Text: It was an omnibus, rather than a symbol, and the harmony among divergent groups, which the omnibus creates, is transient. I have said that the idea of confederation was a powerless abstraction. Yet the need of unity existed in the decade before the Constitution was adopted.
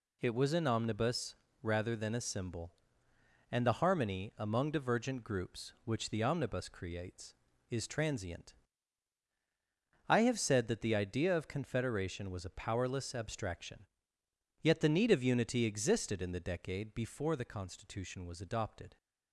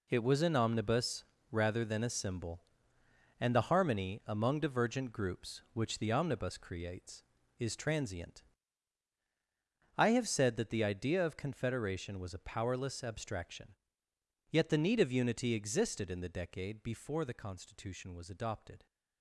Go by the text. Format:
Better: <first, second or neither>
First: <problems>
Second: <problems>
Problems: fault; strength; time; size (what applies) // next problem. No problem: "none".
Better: first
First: none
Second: gets quieter; strong; throughout; 10.5 dB